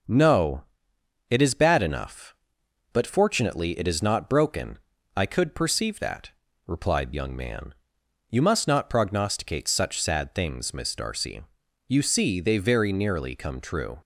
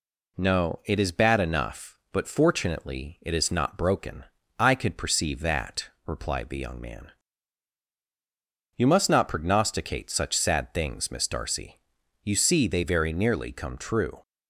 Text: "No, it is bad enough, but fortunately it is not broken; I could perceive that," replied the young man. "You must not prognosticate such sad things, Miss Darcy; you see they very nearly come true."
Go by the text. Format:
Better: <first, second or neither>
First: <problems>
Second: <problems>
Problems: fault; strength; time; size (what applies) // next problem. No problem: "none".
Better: second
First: starts louder than the rest; until 1.7 s; 6.5 dB // skips "the"; at 7.1 s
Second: none